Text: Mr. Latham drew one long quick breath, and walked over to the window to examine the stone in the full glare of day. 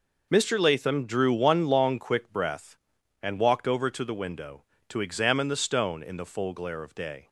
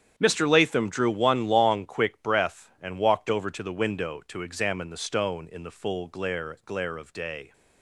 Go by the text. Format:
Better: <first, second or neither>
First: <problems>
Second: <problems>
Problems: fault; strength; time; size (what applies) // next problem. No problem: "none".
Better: first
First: none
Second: starts louder than the rest; strong; until 1.1 s; 8.5 dB // says "glare" twice; at 6.6 s